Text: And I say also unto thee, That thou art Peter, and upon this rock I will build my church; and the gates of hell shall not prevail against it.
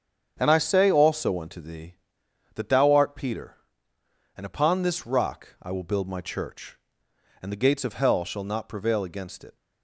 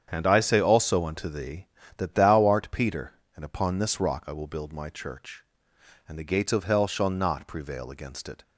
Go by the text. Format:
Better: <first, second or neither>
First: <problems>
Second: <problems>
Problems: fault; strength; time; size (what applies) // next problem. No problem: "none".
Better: neither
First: starts louder than the rest; strong; until 1.4 s; 8 dB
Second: starts louder than the rest; strong; until 1.1 s; 8 dB